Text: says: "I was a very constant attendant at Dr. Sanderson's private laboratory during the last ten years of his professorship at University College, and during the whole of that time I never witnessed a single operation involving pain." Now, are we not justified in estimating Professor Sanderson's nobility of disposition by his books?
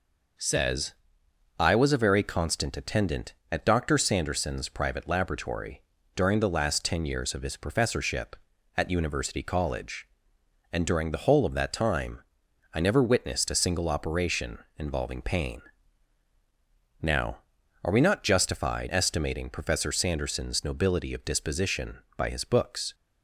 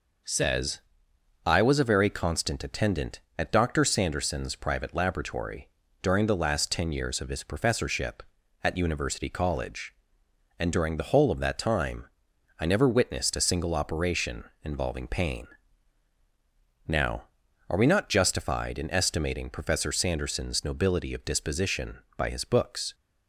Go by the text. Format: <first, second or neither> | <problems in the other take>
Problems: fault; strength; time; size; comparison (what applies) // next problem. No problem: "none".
second | pauses between "laboratory" and "during"; slight; at 5.8 s; 0.32 s long; slight in the second // pauses between "time" and "I"; noticeable; at 12.2 s; 0.54 s long; noticeable in the second // pauses between "operation" and "involving"; slight; at 14.5 s; 0.18 s long; slight in the second // skips "in"; at 18.8 s